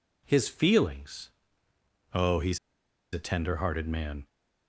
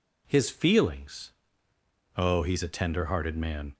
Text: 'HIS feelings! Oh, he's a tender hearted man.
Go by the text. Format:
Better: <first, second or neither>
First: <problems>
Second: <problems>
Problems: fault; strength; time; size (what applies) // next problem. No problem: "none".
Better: second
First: pauses between "he's" and "a"; noticeable; at 2.5 s; 0.55 s long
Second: none